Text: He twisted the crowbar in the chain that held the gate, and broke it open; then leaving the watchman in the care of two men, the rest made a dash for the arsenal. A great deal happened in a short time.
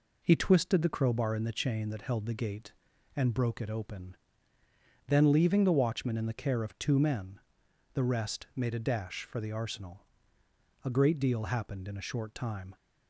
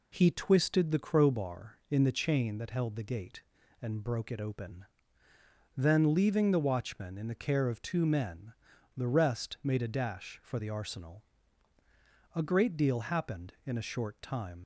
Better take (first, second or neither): first